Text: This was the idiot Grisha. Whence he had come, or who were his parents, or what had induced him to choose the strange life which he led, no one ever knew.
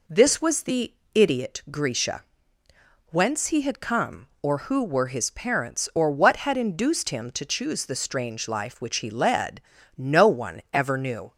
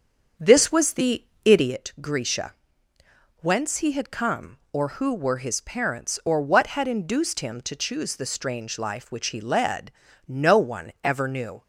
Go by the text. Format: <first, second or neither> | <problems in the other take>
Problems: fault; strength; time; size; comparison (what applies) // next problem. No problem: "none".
first | starts louder than the rest; until 1.9 s; 7 dB // pauses between "the" and "idiot"; slight; at 1.2 s; 0.22 s long; slight in the first